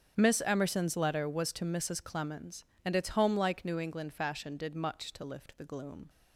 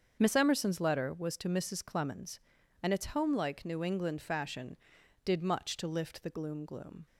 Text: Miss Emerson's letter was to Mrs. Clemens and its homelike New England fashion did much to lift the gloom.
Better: first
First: starts louder than the rest; strong; until 1.1 s; 7.5 dB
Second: starts louder than the rest; until 1.2 s; 7 dB // says "gloom" twice; at 6.6 s

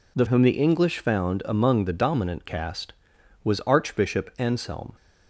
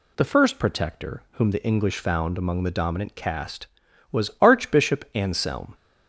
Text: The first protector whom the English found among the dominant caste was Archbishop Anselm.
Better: second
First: skips "first protector"; at 0.2 s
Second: none

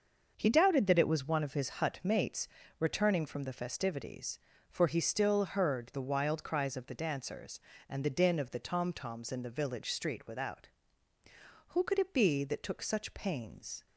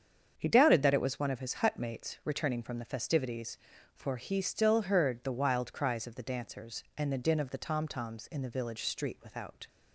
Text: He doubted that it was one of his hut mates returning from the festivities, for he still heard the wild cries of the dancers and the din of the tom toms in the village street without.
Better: second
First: starts louder than the rest; until 1.3 s; 6.5 dB // pauses between "mates" and "returning"; slight; at 2.4 s; 0.30 s long // goes on to say "Who could it be that took such pains"; strong; from 11.6 s on; 2.1 s long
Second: starts louder than the rest; strong; until 1.3 s; 7.5 dB

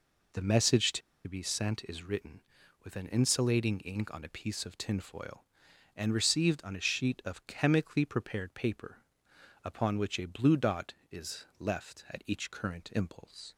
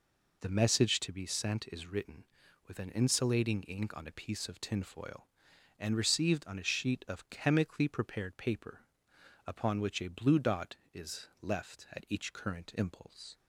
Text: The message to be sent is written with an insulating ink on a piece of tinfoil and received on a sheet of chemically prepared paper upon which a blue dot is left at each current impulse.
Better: second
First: pauses between "to" and "be"; slight; at 1.0 s; 0.26 s long // pauses between "paper" and "upon"; noticeable; at 8.9 s; 0.66 s long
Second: pauses between "paper" and "upon"; noticeable; at 8.8 s; 0.65 s long

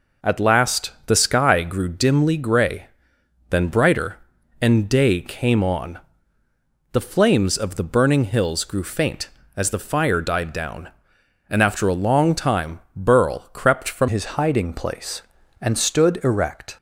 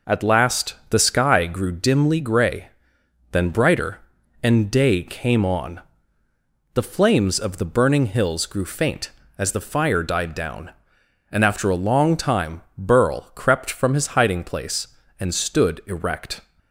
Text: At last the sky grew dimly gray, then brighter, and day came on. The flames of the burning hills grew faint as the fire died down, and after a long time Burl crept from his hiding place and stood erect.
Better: second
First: changes voice at "his"; from 14.0 s on; 2.7 s long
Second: none

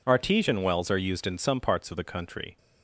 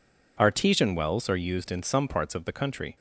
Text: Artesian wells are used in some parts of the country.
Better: neither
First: none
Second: none

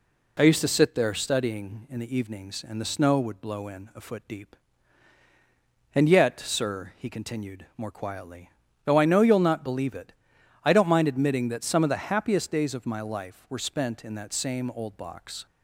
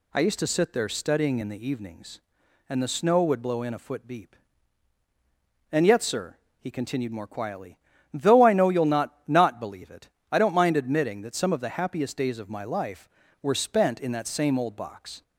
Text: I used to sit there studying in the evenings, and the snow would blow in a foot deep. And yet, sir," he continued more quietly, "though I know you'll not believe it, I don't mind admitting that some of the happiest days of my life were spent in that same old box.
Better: first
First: none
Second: says "not" twice; at 9.2 s

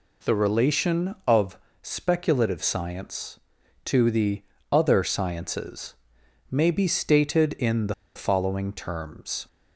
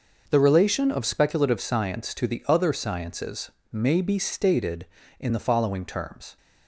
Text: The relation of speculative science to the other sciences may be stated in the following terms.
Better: second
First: pauses between "of" and "speculative"; slight; at 1.5 s; 0.24 s long // pauses between "the" and "other"; slight; at 4.4 s; 0.28 s long // pauses between "sciences" and "may"; noticeable; at 5.9 s; 0.58 s long // pauses between "the" and "following"; slight; at 7.9 s; 0.23 s long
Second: pauses between "sciences" and "may"; slight; at 3.5 s; 0.20 s long

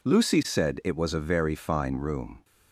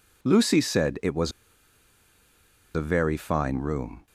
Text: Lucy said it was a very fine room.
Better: first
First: none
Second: pauses between "was" and "a"; strong; at 1.3 s; 1.4 s long

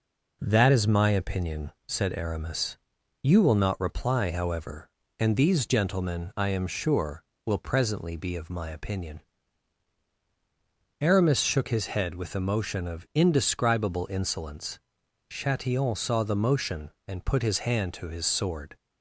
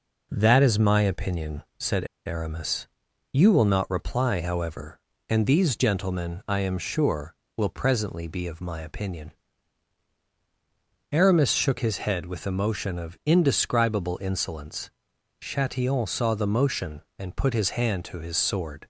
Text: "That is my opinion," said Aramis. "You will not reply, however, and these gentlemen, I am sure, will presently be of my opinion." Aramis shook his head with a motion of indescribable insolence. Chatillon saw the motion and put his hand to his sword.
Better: first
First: none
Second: pauses between "said" and "Aramis"; slight; at 2.0 s; 0.19 s long

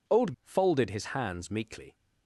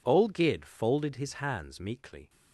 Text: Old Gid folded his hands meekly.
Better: second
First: skips "Gid"; at 0.3 s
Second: none

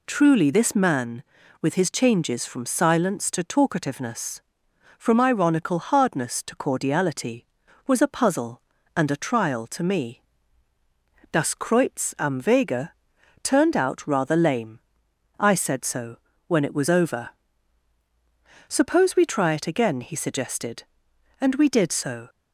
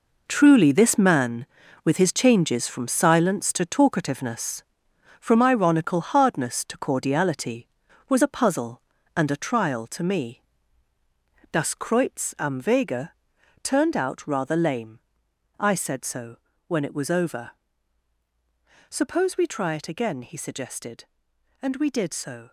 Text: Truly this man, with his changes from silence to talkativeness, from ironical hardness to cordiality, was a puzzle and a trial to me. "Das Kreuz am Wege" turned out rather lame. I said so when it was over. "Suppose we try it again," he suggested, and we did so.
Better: first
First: pauses between "Wege" and "turned"; noticeable; at 12.9 s; 0.52 s long // pauses between "so" and "when"; slight; at 16.1 s; 0.30 s long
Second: gets quieter; strong; throughout; 10 dB // pauses between "Wege" and "turned"; noticeable; at 13.1 s; 0.52 s long // pauses between "so" and "when"; slight; at 16.3 s; 0.30 s long

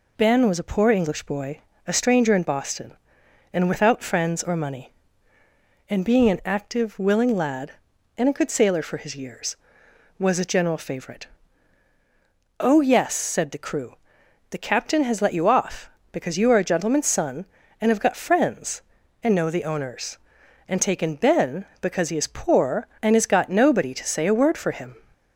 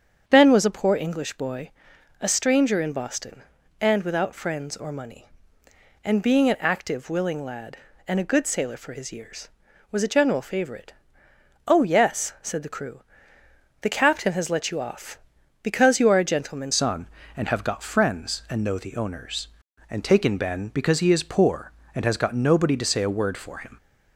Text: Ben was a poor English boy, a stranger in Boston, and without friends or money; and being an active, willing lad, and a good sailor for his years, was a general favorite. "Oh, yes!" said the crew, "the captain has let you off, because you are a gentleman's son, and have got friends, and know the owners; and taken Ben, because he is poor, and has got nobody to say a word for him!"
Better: first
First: none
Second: starts louder than the rest; strong; until 1.2 s; 7.5 dB // changes voice at "son"; from 16.7 s on; 7.0 s long

